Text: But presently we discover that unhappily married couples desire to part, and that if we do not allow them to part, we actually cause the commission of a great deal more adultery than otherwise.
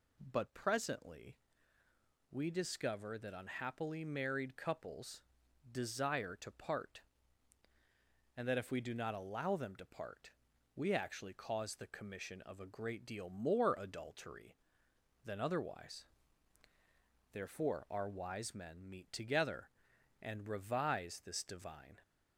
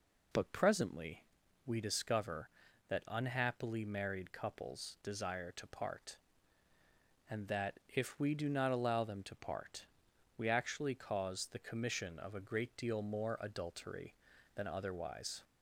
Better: second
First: pauses between "presently" and "we"; noticeable; at 1.3 s; 0.94 s long // pauses between "couples" and "desire"; noticeable; at 5.2 s; 0.46 s long // goes on to say "Therefore our wise men meet together and revise this divine"; strong; from 17.3 s on; 4.6 s long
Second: pauses between "presently" and "we"; at 1.2 s; 0.42 s long

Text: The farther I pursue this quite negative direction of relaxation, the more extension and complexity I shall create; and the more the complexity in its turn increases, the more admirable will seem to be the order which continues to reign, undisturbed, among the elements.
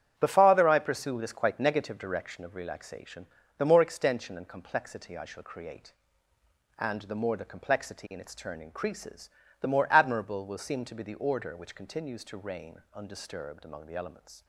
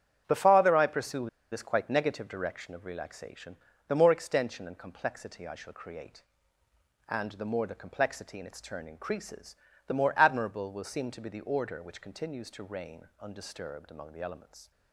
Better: first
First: starts louder than the rest; strong; until 1.1 s; 9.5 dB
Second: starts louder than the rest; strong; until 1.2 s; 9.5 dB // pauses between "pursue" and "this"; slight; at 1.2 s; 0.23 s long

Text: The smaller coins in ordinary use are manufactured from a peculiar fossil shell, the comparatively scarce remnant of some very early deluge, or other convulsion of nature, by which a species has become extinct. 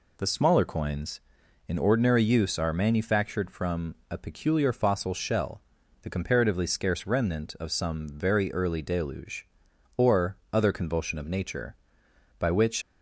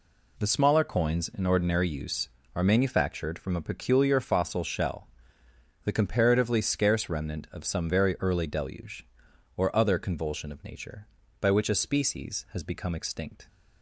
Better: second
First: pauses between "or" and "other"; slight; at 10.3 s; 0.16 s long // stops before "a species has become extinct"; at 12.8 s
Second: none

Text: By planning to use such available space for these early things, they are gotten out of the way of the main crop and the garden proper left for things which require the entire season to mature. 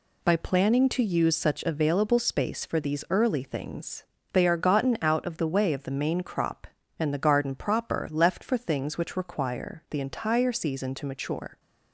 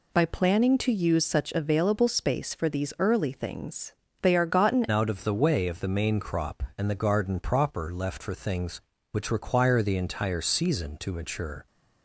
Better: first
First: none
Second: changes voice at "out"; from 4.9 s on; 6.7 s long

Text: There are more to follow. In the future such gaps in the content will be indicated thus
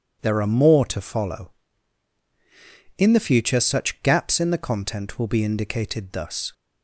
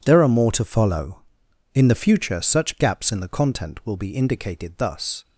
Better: neither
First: none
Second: none

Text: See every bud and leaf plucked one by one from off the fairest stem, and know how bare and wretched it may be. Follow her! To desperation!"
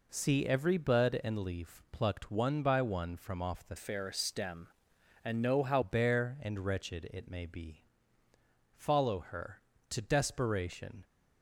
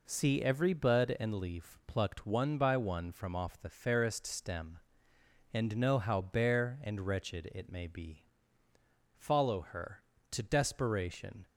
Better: second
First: changes voice from "fairest" to "how"; from 3.7 to 5.8 s; 2.1 s long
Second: none

